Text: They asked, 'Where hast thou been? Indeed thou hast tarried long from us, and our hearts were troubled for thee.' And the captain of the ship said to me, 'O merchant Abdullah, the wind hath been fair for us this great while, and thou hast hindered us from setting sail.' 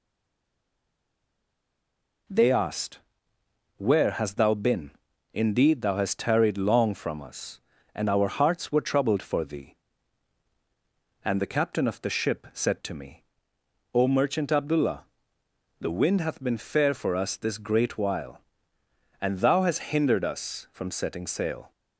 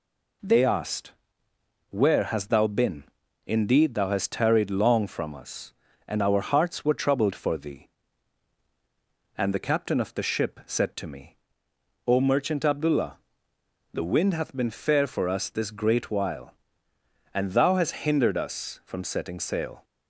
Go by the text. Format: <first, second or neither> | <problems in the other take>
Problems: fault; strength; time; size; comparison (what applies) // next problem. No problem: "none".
second | stays silent before the first word; until 2.2 s; 2.2 s long